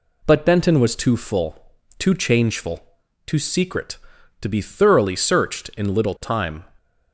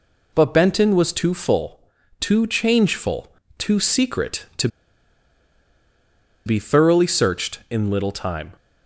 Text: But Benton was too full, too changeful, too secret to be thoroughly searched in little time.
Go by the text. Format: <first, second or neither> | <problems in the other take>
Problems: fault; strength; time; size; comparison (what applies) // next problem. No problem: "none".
first | pauses between "to" and "be"; strong; at 4.6 s; 1.7 s long